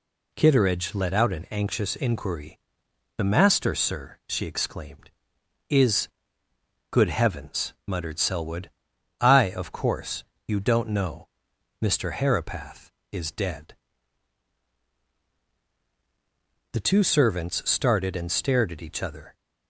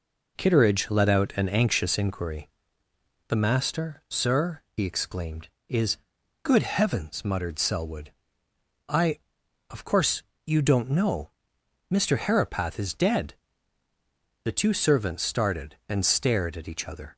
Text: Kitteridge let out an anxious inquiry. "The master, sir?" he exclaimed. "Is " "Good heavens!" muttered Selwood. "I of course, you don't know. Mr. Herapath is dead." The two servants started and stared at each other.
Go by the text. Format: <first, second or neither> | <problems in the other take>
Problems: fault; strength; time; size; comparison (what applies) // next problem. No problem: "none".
second | says "she" for "he"; at 4.2 s